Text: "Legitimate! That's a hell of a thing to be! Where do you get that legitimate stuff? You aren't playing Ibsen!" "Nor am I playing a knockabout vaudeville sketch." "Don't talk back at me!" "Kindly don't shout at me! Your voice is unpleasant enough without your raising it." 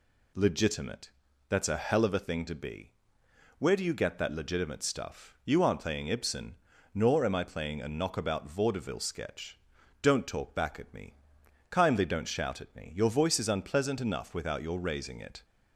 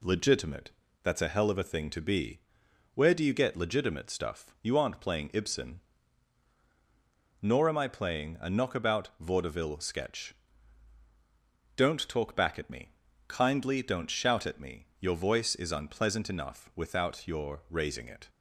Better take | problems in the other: first | skips "that"; at 3.5 s

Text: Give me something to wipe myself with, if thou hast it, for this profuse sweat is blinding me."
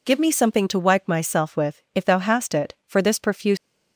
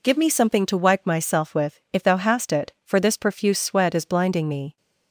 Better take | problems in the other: second | stops before "sweat is blinding me"; at 3.5 s

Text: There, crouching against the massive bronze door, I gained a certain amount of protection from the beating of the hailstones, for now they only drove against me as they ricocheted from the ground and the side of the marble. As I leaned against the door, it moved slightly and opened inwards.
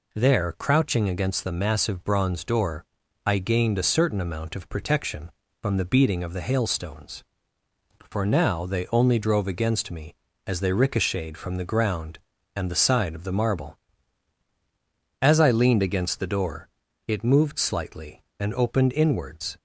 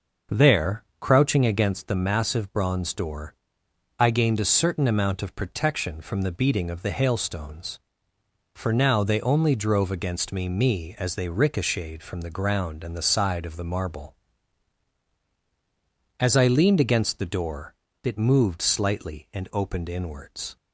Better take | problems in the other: first | starts louder than the rest; noticeable; until 1.4 s; 6 dB // says "me" twice; at 10.4 s

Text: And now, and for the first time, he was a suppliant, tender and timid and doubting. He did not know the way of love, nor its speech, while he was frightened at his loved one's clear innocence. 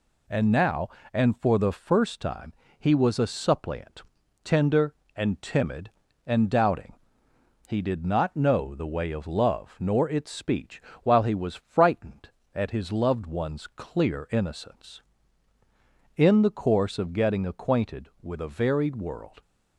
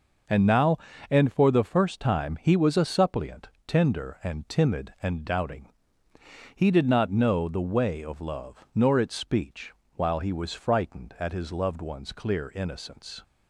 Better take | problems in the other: second | goes on to say "In the course of getting acquainted with a varied world"; strong; from 16.1 s on; 3.2 s long

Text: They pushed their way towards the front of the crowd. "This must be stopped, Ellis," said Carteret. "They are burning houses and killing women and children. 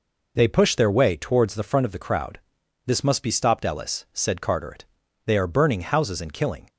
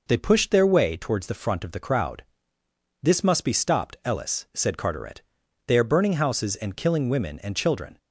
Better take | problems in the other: second | stops before "women and children"; at 6.6 s

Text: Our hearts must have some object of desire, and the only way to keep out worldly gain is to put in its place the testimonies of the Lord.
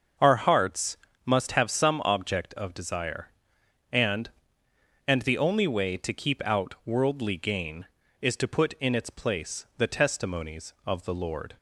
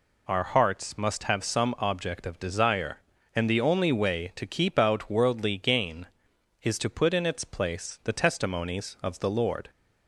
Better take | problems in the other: second | starts louder than the rest; until 1.4 s; 6.5 dB // pauses between "hearts" and "must"; slight; at 0.9 s; 0.28 s long // says "and" twice; at 5.0 s

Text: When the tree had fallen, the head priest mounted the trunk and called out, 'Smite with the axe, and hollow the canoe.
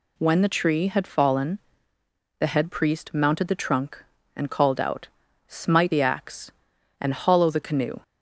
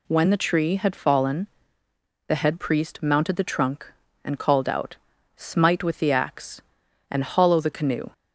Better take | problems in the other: second | skips "with"; at 5.9 s

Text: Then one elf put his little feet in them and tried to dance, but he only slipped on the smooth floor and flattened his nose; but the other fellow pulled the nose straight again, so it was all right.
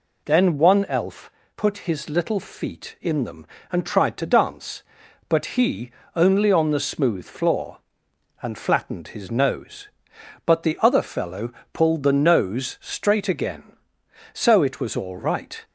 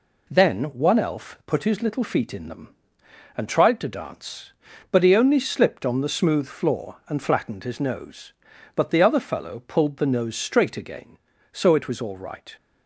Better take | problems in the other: second | pauses between "elf" and "put"; slight; at 1.2 s; 0.26 s long // pauses between "he" and "only"; slight; at 5.9 s; 0.24 s long // skips "slipped"; at 6.5 s // pauses between "fellow" and "pulled"; slight; at 11.5 s; 0.22 s long

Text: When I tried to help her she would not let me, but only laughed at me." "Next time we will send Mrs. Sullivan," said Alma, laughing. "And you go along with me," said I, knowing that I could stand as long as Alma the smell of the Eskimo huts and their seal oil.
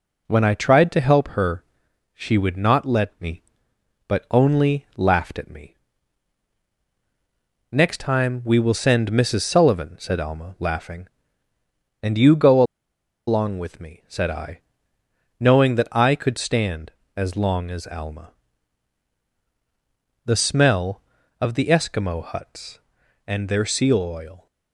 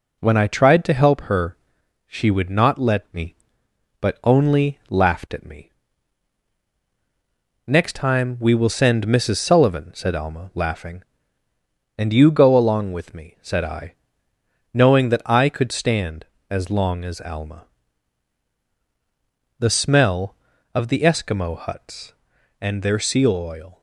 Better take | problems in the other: second | pauses between "her" and "she"; noticeable; at 1.6 s; 0.54 s long; noticeable in the second // pauses between "go" and "along"; noticeable; at 12.6 s; 0.66 s long // pauses between "Alma" and "the"; strong; at 18.3 s; 1.9 s long; strong in the second

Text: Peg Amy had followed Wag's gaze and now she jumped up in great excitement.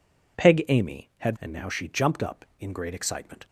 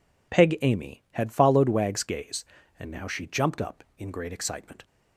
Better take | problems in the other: second | skips "followed Wag's gaze"; at 1.3 s

